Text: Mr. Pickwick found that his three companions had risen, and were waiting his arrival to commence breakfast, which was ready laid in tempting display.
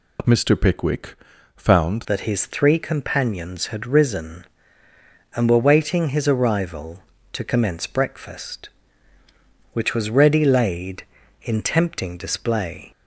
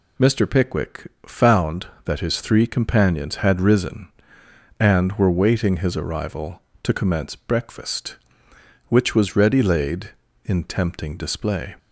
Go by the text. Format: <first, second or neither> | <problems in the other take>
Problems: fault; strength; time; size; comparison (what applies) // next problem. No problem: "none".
second | pauses between "Pickwick" and "found"; at 1.1 s; 0.42 s long; slight in the second // changes voice at "that"; from 2.0 s on; 10.9 s long